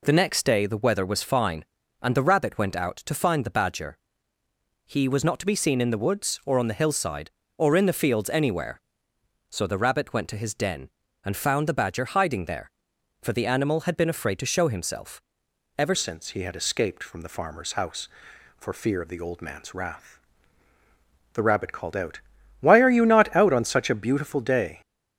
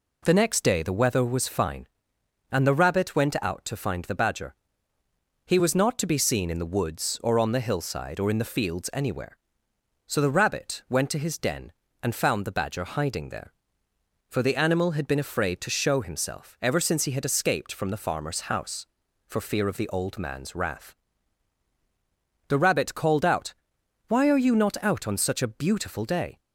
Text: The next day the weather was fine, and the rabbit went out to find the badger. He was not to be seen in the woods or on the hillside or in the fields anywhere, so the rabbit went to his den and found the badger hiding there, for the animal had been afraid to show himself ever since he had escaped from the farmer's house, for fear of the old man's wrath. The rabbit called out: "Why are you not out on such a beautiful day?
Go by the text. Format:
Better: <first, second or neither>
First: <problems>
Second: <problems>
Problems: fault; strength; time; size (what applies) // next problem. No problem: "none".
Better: second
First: pauses between "himself" and "ever"; noticeable; at 15.2 s; 0.56 s long // changes voice at "since"; from 15.9 s on; 8.9 s long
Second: none